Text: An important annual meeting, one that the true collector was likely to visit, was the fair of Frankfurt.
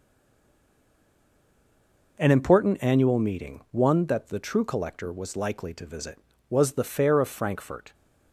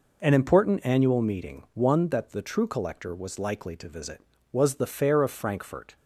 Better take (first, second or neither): second